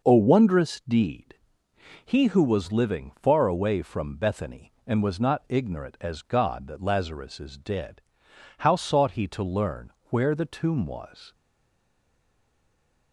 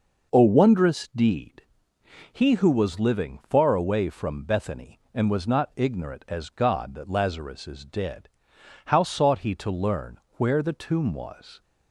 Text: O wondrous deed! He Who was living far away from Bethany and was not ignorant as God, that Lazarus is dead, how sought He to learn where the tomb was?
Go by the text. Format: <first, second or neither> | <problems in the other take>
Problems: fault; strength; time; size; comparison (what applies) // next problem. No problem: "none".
second | pauses between "learn" and "where"; slight; at 9.9 s; 0.18 s long; slight in the second // stays silent after the last word; noticeable; from 11.3 s on; 1.8 s long